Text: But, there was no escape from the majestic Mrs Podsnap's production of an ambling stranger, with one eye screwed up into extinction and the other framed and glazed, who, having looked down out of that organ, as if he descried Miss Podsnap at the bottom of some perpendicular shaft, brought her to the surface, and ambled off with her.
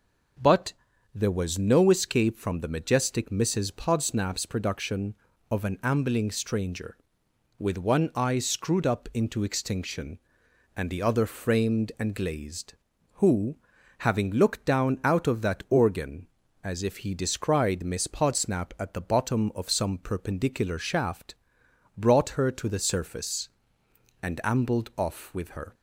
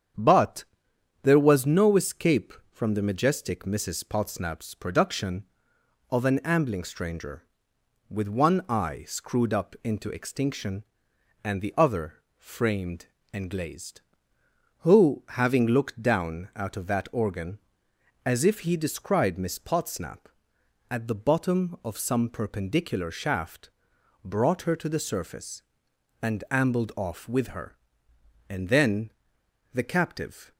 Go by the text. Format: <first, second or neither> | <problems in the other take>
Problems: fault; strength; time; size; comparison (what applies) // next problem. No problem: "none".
first | starts louder than the rest; strong; until 1.7 s; 8 dB // pauses between "other" and "framed"; slight; at 12.1 s; 0.24 s long // goes on to say "And then the captive"; strong; from 28.4 s on; 2.0 s long